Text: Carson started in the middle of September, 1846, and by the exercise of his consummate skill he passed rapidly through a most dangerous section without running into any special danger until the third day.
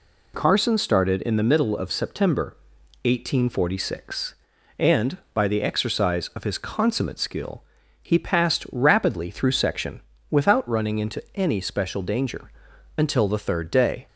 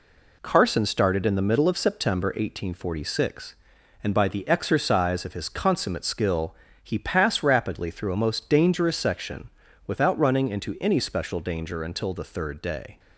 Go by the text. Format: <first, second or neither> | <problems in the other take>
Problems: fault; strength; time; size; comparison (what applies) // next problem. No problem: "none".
second | pauses between "skill" and "he"; at 7.6 s; 0.40 s long; slight in the second // skips "a most dangerous"; at 9.5 s // pauses between "section" and "without"; slight; at 10.0 s; 0.28 s long; slight in the second // pauses between "danger" and "until"; noticeable; at 12.5 s; 0.46 s long